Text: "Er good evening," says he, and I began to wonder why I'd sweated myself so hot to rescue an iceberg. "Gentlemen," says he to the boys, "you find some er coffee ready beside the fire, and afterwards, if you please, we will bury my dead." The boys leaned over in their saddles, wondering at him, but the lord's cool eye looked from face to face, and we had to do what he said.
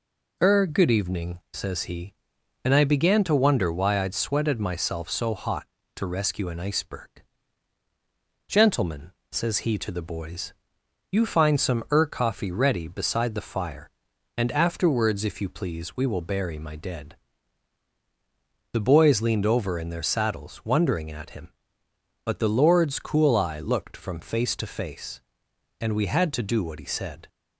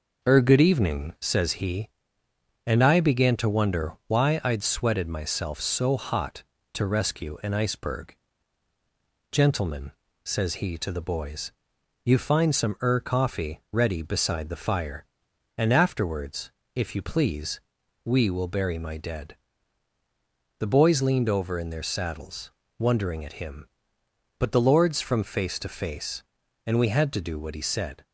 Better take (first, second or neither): first